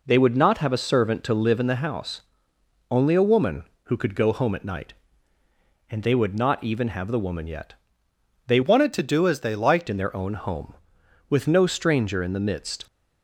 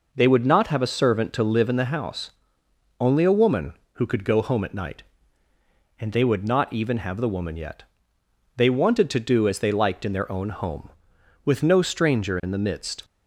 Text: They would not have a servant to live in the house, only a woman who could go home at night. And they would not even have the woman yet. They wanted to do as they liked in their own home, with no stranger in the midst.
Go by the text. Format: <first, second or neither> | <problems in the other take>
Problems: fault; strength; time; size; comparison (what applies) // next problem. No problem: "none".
second | changes voice from "wanted" to "liked"; from 8.6 to 9.8 s; 1.2 s long